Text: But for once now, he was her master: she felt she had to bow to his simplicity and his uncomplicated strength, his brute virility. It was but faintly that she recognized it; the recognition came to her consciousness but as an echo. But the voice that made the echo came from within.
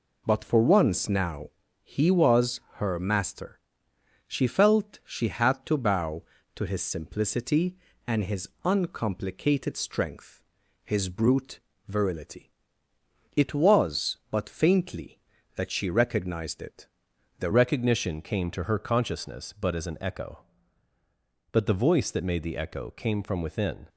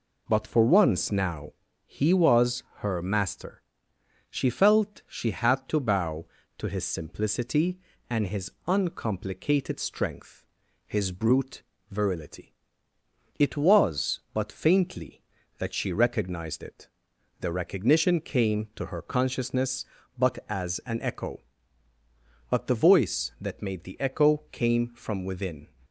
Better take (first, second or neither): second